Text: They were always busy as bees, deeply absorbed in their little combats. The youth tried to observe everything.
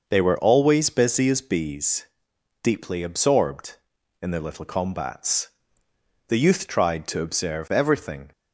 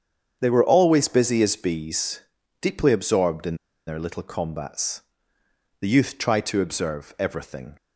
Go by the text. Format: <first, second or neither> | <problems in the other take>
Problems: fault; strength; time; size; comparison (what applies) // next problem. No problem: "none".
first | starts louder than the rest; strong; until 1.4 s; 7.5 dB // pauses between "in" and "their"; slight; at 3.5 s; 0.32 s long